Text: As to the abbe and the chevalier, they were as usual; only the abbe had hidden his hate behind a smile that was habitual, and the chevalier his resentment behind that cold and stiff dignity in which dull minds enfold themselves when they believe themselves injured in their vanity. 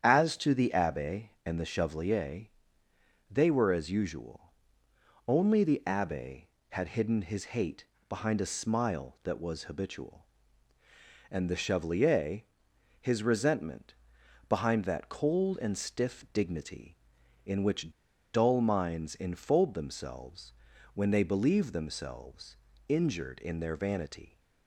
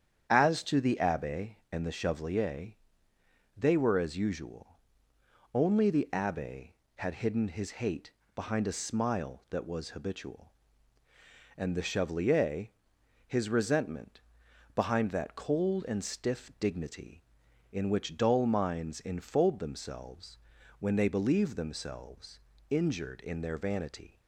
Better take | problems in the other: second | starts louder than the rest; strong; until 1.0 s; 9 dB; strong in the second // pauses between "hate" and "behind"; slight; at 7.8 s; 0.22 s long; slight in the second // pauses between "chevalier" and "his"; noticeable; at 12.4 s; 0.58 s long; noticeable in the second // pauses between "resentment" and "behind"; noticeable; at 13.9 s; 0.52 s long; noticeable in the second // pauses between "which" and "dull"; at 17.9 s; 0.43 s long // pauses between "themselves" and "when"; at 20.5 s; 0.40 s long; also in the second // pauses between "themselves" and "injured"; slight; at 22.5 s; 0.32 s long; slight in the second

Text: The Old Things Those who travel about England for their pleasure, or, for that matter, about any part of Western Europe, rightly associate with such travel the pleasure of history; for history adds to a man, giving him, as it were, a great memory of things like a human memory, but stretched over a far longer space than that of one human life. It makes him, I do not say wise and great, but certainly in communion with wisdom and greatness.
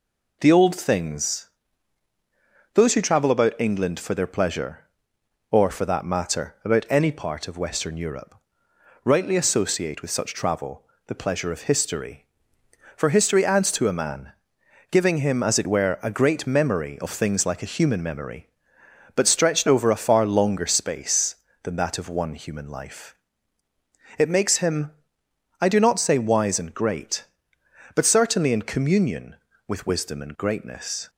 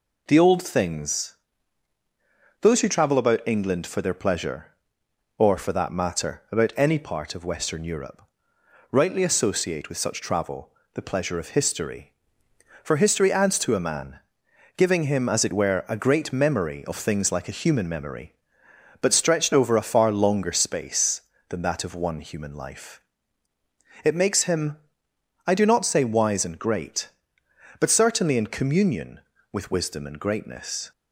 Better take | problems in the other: neither | pauses between "Things" and "Those"; strong; the same in both // pauses between "travel" and "the"; slight; the same in both

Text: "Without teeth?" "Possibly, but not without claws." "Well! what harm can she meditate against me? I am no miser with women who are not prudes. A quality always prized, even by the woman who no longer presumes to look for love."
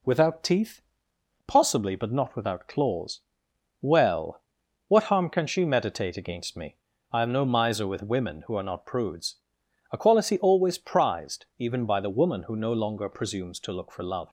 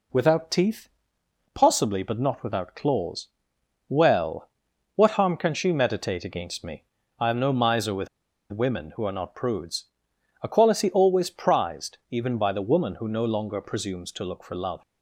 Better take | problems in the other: first | pauses between "with" and "women"; at 8.0 s; 0.43 s long

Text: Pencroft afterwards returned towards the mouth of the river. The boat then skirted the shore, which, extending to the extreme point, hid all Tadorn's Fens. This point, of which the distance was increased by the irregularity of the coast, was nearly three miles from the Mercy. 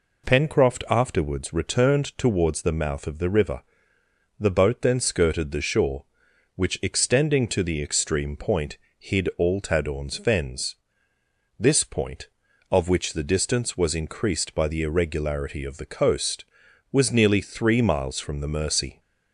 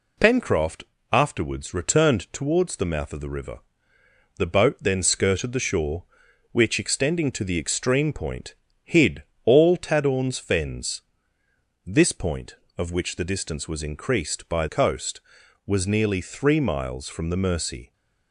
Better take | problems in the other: first | pauses between "Pencroft" and "afterwards"; slight; at 0.8 s; 0.30 s long // pauses between "hid" and "all"; slight; at 9.2 s; 0.22 s long // skips "the irregularity of the"; at 14.6 s

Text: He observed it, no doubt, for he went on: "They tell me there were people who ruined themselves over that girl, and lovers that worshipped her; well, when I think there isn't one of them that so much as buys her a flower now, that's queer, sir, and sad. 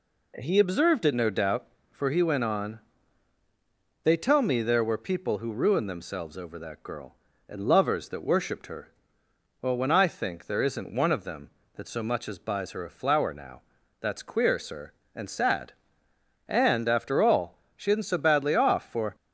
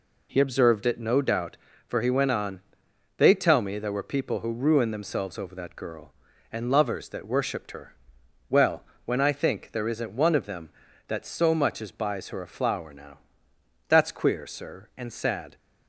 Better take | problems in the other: second | goes on to say "And after all she isn't so badly off for"; strong; from 16.4 s on; 2.6 s long

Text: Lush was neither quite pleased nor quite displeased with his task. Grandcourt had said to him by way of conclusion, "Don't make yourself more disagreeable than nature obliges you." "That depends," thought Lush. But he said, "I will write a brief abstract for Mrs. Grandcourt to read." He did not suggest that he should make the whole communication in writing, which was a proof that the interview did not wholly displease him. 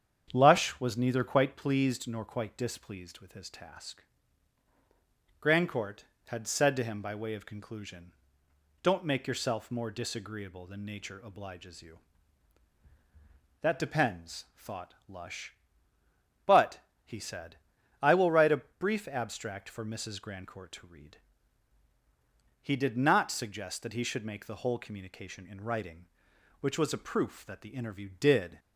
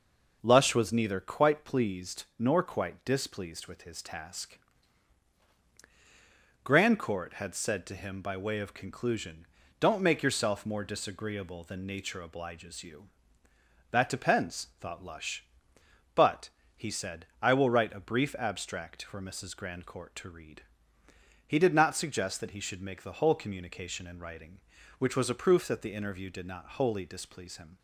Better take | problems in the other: second | starts louder than the rest; strong; until 1.3 s; 8 dB // pauses between "But" and "he"; slight; at 16.8 s; 0.24 s long; slight in the second // stops before "not wholly displease him"; at 28.5 s

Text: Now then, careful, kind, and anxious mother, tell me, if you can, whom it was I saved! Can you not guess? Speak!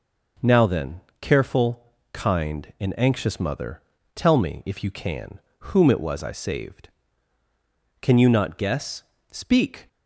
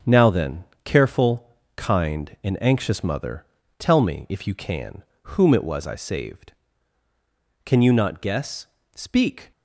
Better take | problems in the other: first | gets quieter; strong; throughout; 7 dB

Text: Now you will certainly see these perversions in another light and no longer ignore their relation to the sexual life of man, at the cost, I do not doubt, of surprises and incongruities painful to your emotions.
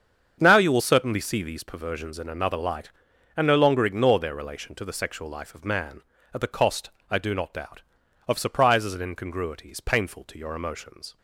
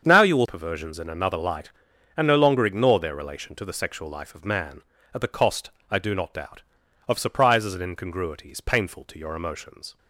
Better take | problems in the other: first | starts louder than the rest; strong; until 1.0 s; 7 dB; strong in the first // skips "certainly see these"; at 0.4 s

